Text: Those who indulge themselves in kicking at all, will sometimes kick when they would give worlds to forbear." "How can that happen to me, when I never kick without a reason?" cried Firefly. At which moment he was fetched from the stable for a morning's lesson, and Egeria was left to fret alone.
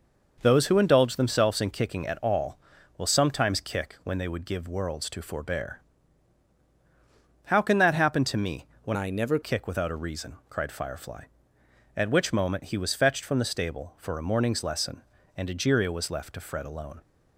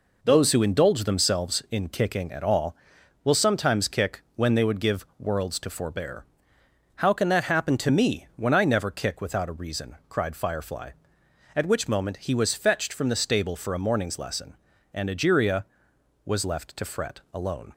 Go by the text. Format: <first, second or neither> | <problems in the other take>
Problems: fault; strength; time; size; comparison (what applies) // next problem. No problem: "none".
second | changes voice from "I" to "never"; from 8.9 to 9.3 s; 0.4 s long